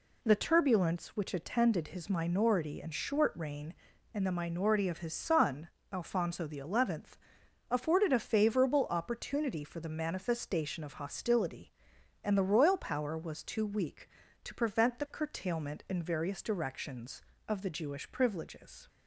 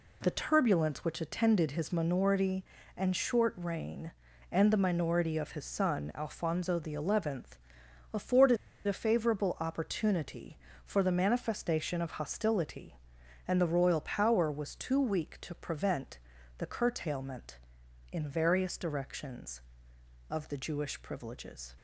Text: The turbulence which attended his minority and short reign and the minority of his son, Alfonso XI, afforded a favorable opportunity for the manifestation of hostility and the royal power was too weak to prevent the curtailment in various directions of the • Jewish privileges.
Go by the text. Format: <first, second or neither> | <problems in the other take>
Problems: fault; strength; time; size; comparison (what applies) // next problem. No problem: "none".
first | pauses between "afforded" and "a"; slight; at 8.5 s; 0.31 s long // pauses between "prevent" and "the"; at 16.1 s; 0.40 s long